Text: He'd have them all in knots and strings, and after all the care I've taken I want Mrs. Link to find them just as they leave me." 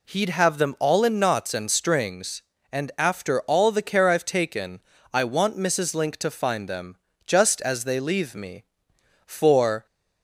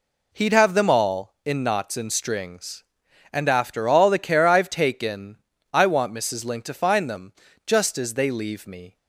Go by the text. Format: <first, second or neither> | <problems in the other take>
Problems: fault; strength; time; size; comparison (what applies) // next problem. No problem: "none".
second | pauses between "taken" and "I"; slight; at 4.7 s; 0.34 s long; slight in the second // pauses between "them" and "just"; slight; at 6.9 s; 0.30 s long; slight in the second // goes on to say "For"; from 9.2 s on; 0.60 s long